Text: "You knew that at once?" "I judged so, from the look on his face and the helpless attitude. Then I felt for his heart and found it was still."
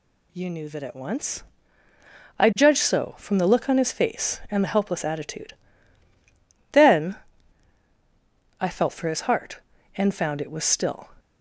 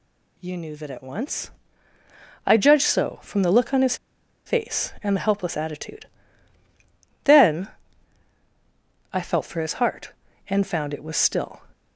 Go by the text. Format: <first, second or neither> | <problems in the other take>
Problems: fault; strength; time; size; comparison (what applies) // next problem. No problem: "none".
first | pauses between "his" and "face"; noticeable; at 3.9 s; 0.50 s long // pauses between "Then" and "I"; strong; at 7.6 s; 1.4 s long; strong in the first